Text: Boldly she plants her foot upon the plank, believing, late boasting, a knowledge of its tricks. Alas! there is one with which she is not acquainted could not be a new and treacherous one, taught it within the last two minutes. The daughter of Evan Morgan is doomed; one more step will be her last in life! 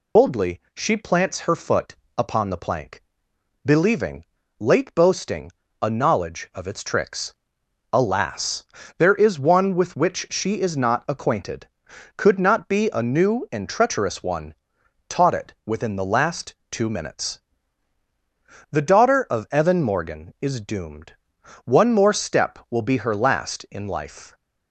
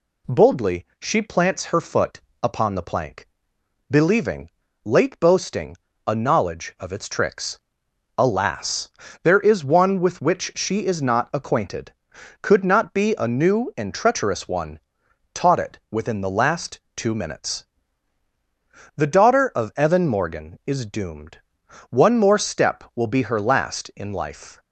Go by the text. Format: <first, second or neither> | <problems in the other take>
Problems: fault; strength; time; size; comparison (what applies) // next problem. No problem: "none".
second | loses the start of "Boldly"; at 0.1 s; 150 ms // pauses between "foot" and "upon"; slight; at 1.9 s; 0.22 s long; slight in the second // pauses between "last" and "two"; slight; at 16.5 s; 0.16 s long; slight in the second